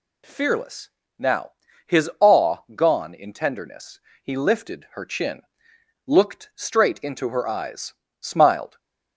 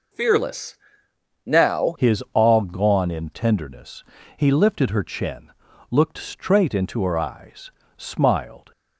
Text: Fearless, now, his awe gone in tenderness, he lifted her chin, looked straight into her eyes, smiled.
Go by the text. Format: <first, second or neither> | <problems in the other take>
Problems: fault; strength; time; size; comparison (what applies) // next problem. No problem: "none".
first | changes voice at "his"; from 1.9 s on; 6.8 s long